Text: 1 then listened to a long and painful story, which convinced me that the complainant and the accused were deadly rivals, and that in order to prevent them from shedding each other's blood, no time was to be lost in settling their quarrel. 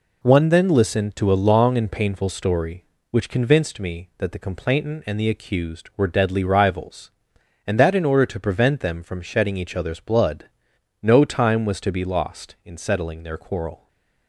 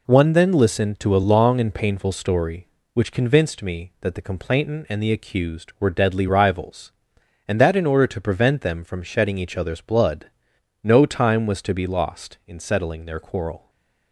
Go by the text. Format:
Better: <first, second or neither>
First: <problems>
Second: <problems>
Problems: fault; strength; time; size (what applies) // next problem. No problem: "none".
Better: neither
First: stays silent after the last word; slight; from 13.7 s on; 0.5 s long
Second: stays silent after the last word; slight; from 13.5 s on; 0.6 s long